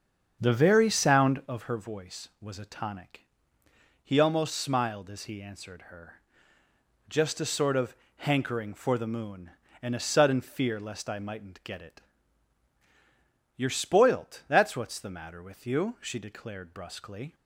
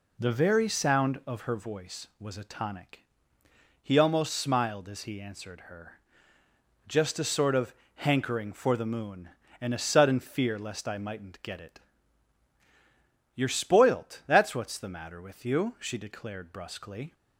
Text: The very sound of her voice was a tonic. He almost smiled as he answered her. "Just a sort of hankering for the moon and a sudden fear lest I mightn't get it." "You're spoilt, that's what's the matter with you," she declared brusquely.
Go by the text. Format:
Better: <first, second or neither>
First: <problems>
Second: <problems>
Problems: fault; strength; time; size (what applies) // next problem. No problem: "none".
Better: second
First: starts louder than the rest; strong; until 1.6 s; 7 dB // pauses between "of" and "hankering"; slight; at 7.9 s; 0.22 s long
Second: pauses between "of" and "hankering"; slight; at 7.7 s; 0.22 s long